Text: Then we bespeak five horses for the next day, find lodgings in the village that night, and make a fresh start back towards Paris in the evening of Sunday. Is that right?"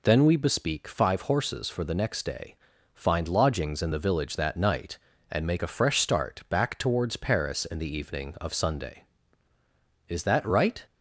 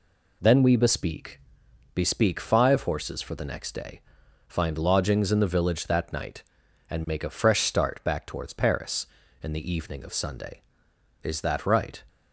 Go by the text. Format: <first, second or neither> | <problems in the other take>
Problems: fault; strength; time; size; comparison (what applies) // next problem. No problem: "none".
first | says "bespeak" twice; at 1.9 s